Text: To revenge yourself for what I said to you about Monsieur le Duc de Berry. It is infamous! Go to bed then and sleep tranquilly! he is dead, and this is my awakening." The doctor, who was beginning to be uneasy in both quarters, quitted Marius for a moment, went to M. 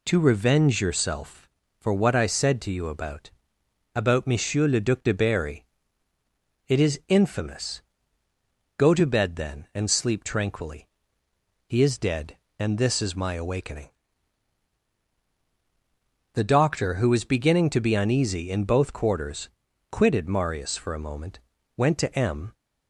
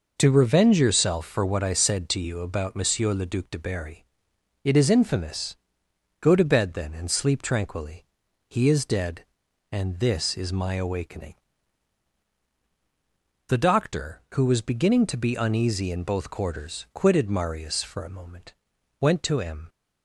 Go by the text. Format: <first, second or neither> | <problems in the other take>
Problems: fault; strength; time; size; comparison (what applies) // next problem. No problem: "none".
second | says "about" twice; at 3.9 s